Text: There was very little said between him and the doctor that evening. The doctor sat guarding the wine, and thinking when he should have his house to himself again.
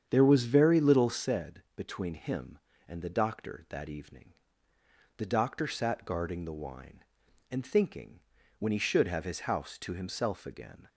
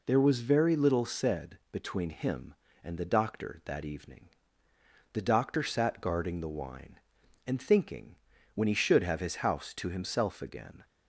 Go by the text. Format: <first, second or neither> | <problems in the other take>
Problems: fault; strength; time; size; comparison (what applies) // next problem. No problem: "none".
second | starts louder than the rest; strong; until 1.3 s; 8 dB // pauses between "thinking" and "when"; at 8.2 s; 0.38 s long; also in the second